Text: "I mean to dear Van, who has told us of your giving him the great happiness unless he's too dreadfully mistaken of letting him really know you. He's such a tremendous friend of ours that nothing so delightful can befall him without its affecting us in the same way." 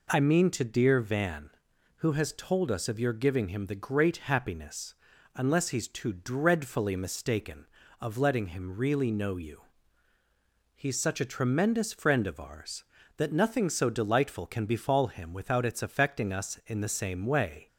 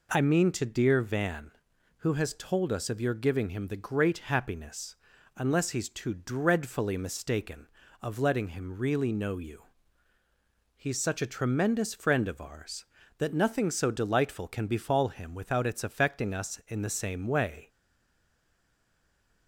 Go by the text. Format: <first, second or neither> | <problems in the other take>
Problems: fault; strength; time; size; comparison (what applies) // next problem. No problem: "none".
first | pauses between "happiness" and "unless"; at 4.9 s; 0.40 s long; also in the first // stays silent after the last word; noticeable; from 17.6 s on; 1.8 s long